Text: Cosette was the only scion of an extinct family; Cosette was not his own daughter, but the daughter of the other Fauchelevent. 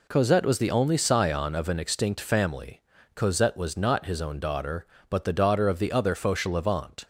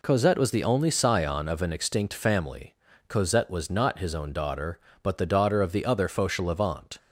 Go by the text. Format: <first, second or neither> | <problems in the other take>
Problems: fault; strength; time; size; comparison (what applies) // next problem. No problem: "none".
neither | none